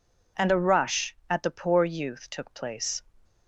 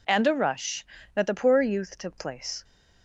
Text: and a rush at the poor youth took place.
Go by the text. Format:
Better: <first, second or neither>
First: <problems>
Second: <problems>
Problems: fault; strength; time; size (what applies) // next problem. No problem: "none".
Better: first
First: none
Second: says "that" for "at"; at 1.1 s